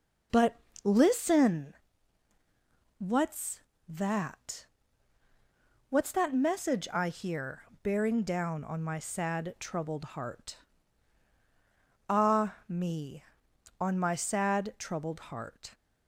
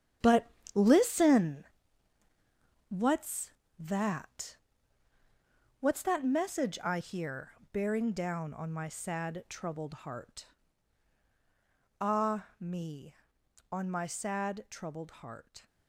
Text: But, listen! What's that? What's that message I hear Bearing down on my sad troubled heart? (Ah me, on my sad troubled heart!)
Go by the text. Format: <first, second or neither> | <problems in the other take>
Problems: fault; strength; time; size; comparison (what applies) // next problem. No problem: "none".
first | gets quieter; strong; throughout; 10 dB // pauses between "hear" and "Bearing"; slight; at 7.5 s; 0.20 s long; slight in the first